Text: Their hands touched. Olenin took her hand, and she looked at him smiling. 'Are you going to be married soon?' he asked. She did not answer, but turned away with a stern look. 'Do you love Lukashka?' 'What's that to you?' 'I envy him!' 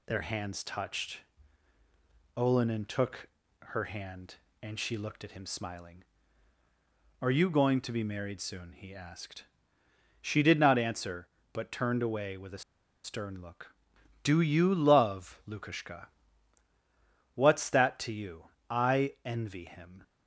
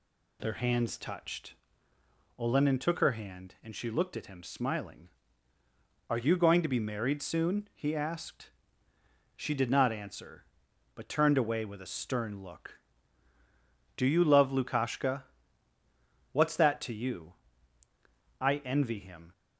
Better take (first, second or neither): second